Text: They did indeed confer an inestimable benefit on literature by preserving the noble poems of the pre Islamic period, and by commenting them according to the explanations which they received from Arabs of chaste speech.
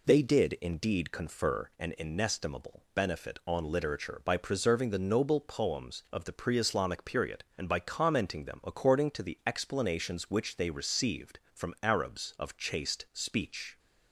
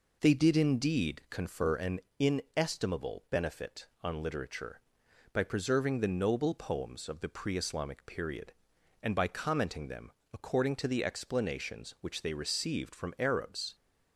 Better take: first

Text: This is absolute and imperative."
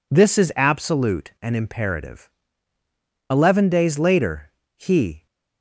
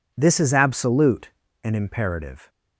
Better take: second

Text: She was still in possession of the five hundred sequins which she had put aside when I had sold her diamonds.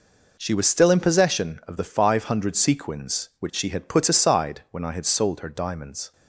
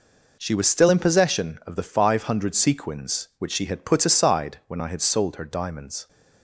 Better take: neither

